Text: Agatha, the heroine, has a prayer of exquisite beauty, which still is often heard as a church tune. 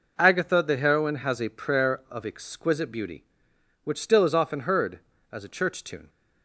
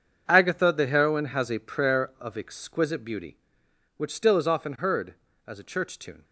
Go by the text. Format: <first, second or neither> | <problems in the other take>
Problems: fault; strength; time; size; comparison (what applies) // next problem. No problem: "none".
first | gets quieter; strong; throughout; 14 dB